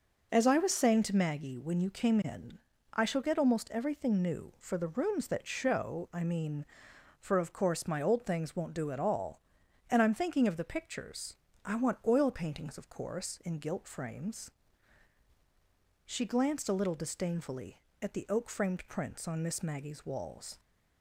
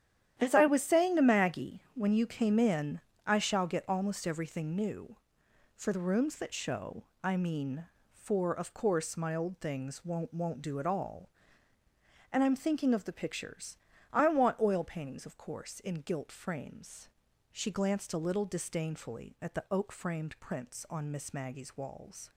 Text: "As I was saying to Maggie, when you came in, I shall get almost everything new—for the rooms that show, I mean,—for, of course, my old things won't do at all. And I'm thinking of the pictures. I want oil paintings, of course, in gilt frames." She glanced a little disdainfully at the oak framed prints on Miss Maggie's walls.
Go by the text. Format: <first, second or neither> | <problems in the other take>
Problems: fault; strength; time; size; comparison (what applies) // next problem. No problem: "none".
first | starts louder than the rest; strong; until 1.4 s; 10.5 dB // says "won't" twice; at 10.3 s